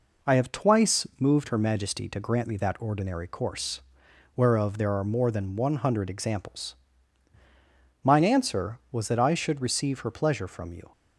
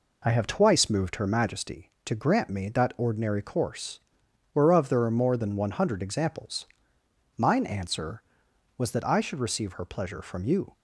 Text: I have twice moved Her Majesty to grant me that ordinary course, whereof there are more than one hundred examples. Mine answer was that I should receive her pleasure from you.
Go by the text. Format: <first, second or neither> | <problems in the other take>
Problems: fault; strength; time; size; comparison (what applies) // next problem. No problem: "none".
neither | none